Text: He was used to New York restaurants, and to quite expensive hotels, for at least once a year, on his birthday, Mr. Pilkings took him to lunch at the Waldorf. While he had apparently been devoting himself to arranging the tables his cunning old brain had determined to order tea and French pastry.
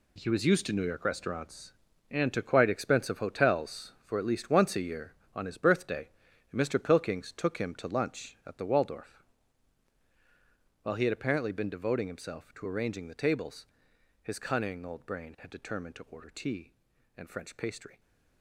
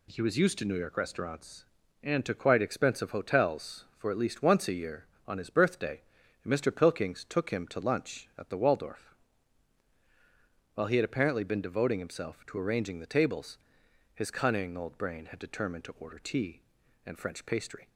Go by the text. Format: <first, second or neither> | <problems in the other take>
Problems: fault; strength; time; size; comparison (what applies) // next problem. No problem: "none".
second | gets quieter; strong; throughout; 11 dB // pauses between "tables" and "his"; noticeable; at 13.6 s; 0.56 s long; noticeable in the second